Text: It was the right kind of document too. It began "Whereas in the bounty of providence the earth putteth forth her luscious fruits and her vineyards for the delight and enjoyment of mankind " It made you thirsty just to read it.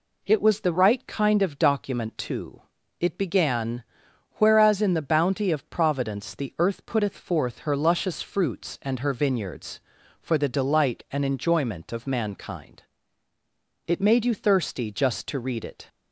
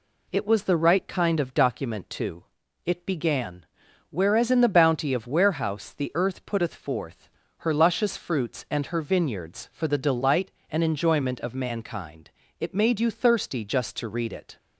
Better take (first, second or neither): first